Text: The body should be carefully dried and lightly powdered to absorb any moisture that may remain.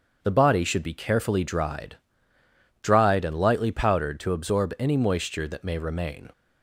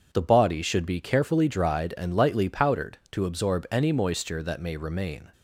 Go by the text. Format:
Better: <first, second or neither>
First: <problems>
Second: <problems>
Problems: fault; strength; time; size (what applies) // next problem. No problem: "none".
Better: second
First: starts louder than the rest; until 1.2 s; 6.5 dB // says "dried" twice; at 2.8 s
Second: none